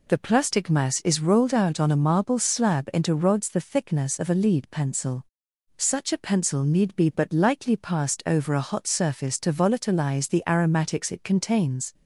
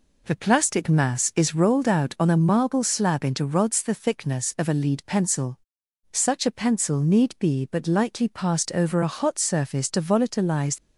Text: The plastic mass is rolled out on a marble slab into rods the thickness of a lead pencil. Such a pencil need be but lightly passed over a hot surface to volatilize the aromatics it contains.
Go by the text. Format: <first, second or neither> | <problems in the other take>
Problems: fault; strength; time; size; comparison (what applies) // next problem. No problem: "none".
first | stops before "the aromatics it contains"; at 10.7 s